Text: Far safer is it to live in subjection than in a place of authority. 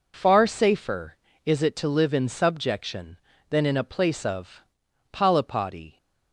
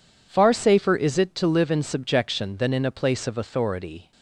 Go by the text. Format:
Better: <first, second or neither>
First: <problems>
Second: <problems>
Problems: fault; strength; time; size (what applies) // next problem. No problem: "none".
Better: second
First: says "polypody" for "authority"; at 5.1 s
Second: none